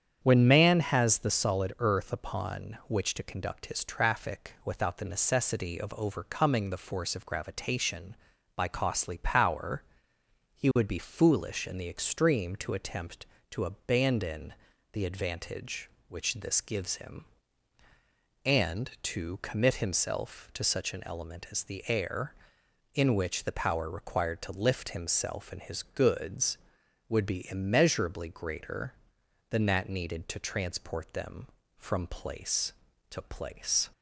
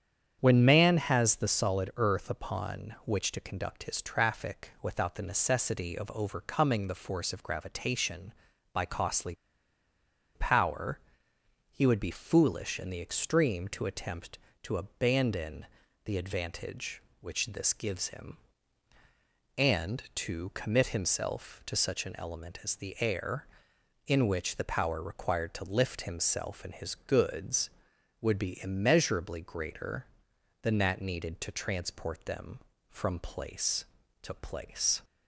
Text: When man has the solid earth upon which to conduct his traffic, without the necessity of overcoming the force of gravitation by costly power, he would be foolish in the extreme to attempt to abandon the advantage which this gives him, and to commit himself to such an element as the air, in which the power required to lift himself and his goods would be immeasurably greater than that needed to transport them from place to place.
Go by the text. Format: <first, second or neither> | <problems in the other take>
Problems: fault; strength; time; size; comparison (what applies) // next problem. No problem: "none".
first | starts louder than the rest; strong; until 1.4 s; 8 dB; strong in the first // pauses between "costly" and "power"; at 9.3 s; 1.0 s long // pauses between "abandon" and "the"; at 15.6 s; 0.38 s long; also in the first